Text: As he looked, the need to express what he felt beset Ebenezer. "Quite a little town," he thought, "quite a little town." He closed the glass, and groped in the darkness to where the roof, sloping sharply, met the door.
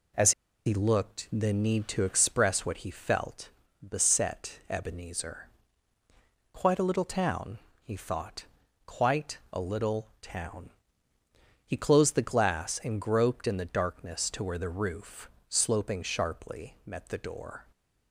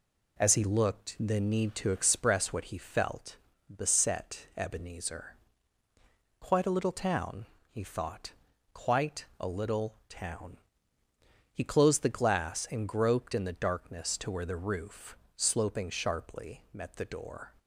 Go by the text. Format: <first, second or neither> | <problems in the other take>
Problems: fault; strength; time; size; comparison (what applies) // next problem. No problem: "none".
second | pauses between "As" and "he"; slight; at 0.3 s; 0.35 s long // pauses between "felt" and "beset"; at 3.4 s; 0.38 s long; also in the second